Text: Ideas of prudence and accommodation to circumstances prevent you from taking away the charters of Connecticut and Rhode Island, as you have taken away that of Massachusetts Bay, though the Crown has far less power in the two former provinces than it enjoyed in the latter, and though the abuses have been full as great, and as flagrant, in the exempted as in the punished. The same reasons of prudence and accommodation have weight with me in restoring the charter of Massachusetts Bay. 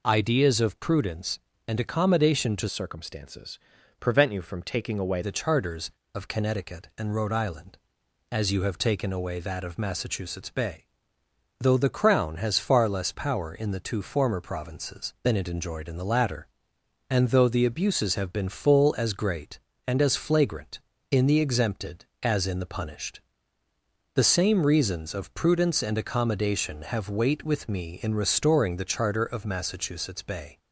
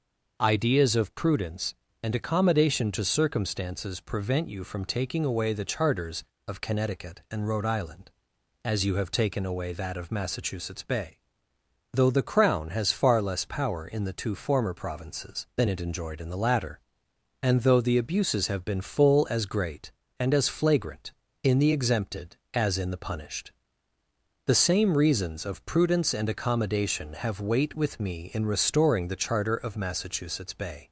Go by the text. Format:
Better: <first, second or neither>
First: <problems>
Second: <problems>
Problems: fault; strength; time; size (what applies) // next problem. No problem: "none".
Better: second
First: changes voice from "circumstances" to "away"; from 2.6 to 5.2 s; 2.6 s long // pauses between "circumstances" and "prevent"; at 3.5 s; 0.42 s long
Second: none